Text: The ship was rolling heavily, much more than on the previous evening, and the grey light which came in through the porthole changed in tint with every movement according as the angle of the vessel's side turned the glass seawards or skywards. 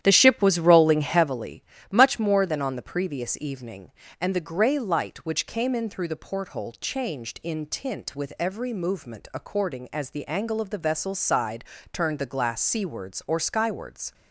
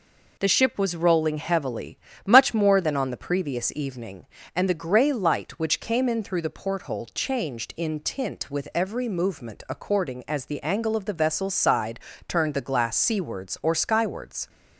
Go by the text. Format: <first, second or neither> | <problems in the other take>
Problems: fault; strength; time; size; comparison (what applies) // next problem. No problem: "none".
second | starts louder than the rest; strong; until 1.4 s; 11 dB // pauses between "side" and "turned"; slight; at 11.6 s; 0.30 s long; slight in the second